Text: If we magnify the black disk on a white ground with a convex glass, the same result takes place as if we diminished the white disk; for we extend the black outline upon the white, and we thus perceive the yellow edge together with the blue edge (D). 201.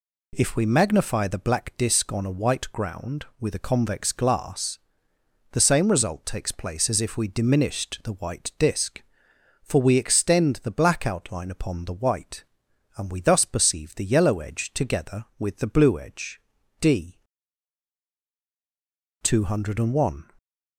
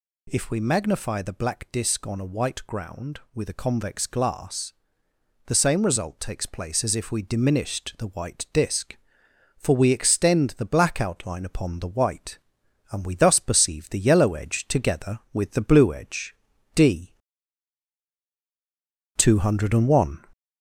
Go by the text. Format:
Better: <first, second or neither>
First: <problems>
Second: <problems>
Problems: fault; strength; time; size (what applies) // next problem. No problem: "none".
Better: first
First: none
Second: gets louder; slight; throughout; 3 dB